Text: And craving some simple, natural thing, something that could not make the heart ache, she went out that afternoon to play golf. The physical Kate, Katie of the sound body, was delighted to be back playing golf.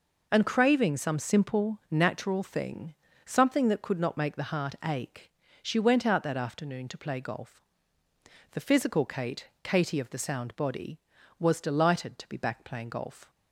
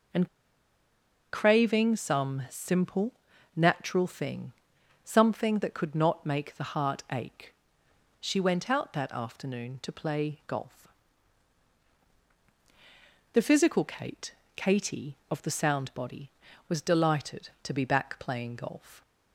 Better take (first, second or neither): first